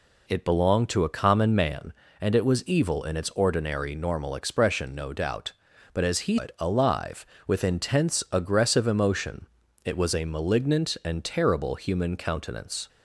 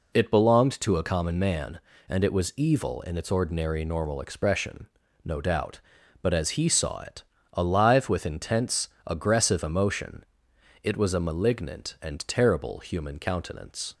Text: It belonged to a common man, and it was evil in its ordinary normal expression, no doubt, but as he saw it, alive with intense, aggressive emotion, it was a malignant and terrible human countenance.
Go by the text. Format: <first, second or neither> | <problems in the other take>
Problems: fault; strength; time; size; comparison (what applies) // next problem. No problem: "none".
second | skips "saw"; at 6.3 s